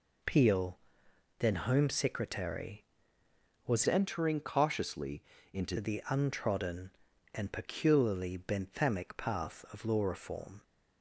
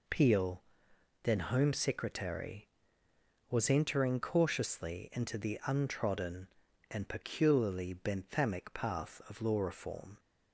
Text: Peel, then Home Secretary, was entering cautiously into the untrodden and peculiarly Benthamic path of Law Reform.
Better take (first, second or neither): second